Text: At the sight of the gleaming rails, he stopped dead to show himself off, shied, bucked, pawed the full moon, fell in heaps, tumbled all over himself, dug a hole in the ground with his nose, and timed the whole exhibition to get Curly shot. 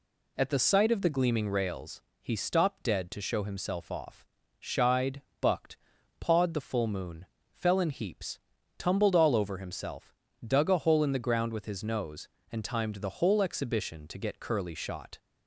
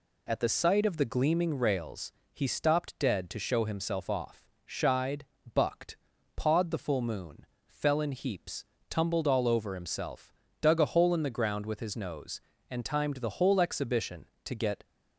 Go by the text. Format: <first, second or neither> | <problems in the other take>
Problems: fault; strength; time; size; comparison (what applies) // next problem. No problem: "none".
first | stops before "Curly shot"; at 14.8 s